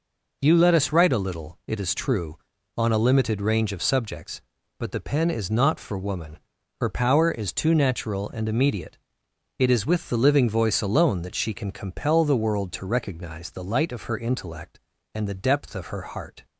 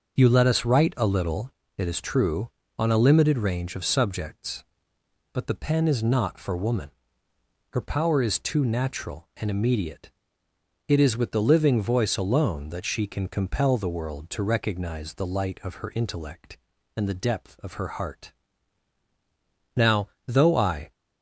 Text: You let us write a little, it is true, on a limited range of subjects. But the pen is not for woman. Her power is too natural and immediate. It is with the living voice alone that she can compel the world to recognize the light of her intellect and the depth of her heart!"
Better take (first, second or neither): first